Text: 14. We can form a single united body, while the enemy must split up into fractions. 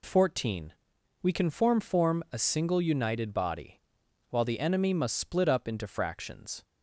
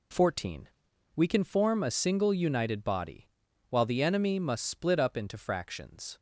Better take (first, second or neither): second